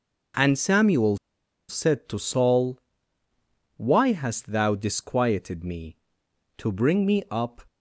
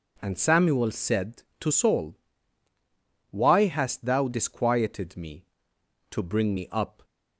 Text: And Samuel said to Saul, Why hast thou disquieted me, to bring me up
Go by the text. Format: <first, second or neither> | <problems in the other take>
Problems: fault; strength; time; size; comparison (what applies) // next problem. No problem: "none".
second | pauses between "Samuel" and "said"; noticeable; at 1.1 s; 0.53 s long